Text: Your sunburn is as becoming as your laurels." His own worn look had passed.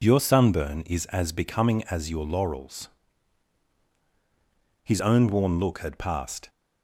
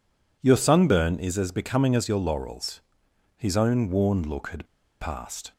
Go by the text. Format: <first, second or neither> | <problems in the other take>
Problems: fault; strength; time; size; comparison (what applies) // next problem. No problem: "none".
first | pauses between "had" and "passed"; slight; at 4.6 s; 0.34 s long